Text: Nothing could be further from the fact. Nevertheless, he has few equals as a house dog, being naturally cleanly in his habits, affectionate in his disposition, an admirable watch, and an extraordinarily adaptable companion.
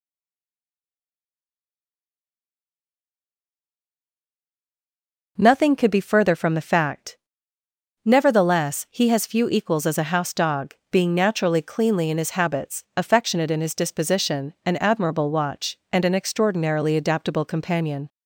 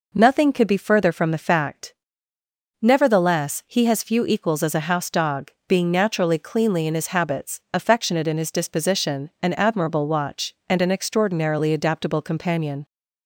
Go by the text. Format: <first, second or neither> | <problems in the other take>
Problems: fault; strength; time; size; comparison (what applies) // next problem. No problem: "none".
second | stays silent before the first word; strong; until 5.3 s; 5.3 s long